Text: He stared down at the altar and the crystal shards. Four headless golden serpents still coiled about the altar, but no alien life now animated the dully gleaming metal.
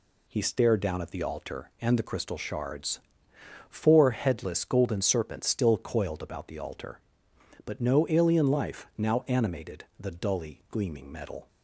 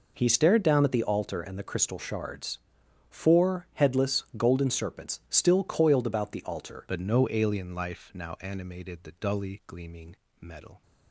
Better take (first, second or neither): first